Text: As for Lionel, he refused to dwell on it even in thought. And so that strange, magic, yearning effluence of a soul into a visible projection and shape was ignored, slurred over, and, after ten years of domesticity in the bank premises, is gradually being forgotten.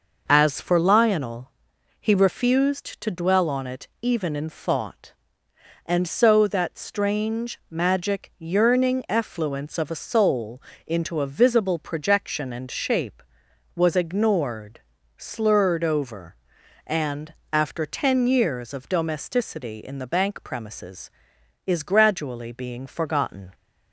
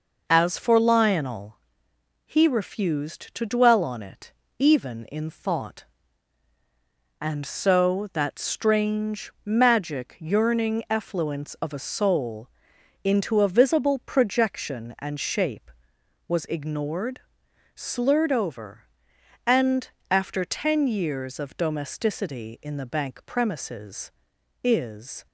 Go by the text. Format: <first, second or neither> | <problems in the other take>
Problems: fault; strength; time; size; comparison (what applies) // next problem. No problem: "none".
first | pauses between "it" and "even"; slight; at 4.3 s; 0.26 s long; slight in the first // pauses between "soul" and "into"; noticeable; at 12.4 s; 0.56 s long; slight in the first // stops before "gradually being forgotten"; at 25.2 s